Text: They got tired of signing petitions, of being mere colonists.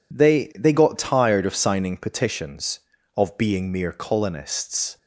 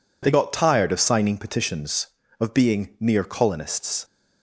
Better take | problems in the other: second | says "They" twice; at 0.5 s

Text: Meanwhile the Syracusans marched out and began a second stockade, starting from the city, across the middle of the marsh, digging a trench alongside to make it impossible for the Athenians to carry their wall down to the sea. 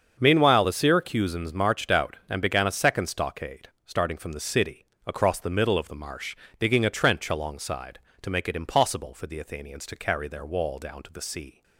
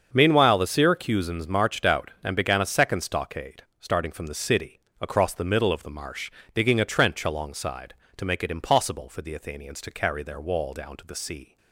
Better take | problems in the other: neither | starts louder than the rest; the same in both

